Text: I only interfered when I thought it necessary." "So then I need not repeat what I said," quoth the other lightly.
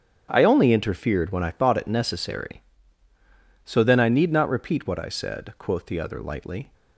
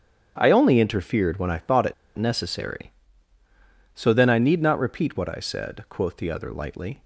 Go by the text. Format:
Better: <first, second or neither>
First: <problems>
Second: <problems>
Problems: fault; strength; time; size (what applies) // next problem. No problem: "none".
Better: first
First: starts louder than the rest; strong; until 1.3 s; 8 dB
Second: starts louder than the rest; strong; until 1.3 s; 8 dB // pauses between "it" and "necessary"; slight; at 1.9 s; 0.23 s long